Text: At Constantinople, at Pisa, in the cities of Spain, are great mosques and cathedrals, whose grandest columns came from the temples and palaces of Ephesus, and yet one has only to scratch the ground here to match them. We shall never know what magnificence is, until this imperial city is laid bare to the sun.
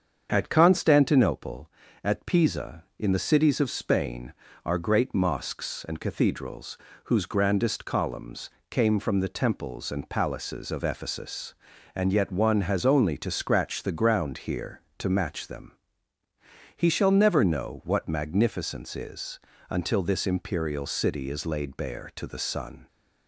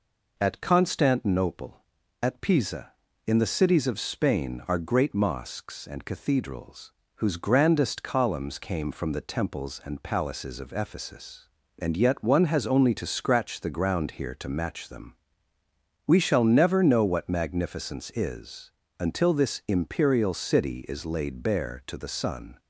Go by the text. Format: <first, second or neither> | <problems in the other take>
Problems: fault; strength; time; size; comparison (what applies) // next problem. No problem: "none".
second | starts louder than the rest; strong; until 1.3 s; 7.5 dB // pauses between "columns" and "came"; slight; at 8.4 s; 0.20 s long // says "He" for "We"; at 16.7 s